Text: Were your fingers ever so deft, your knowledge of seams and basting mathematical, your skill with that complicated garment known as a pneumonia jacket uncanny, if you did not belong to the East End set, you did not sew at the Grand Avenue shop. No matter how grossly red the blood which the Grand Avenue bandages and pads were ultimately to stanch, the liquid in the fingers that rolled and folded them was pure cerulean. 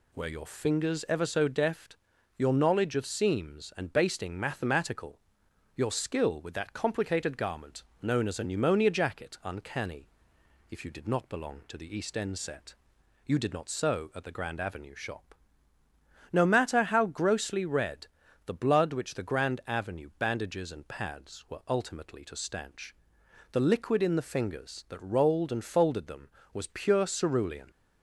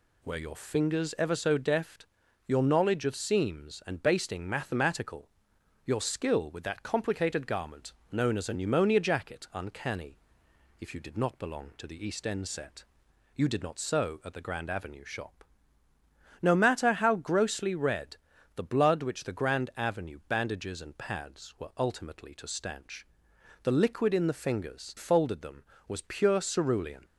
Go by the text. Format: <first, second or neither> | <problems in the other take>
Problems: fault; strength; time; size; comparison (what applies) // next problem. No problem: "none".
first | pauses between "garment" and "known"; slight; at 7.9 s; 0.20 s long; slight in the first // pauses between "red" and "the"; slight; at 18.1 s; 0.36 s long; slight in the first // skips "that rolled and"; at 24.9 s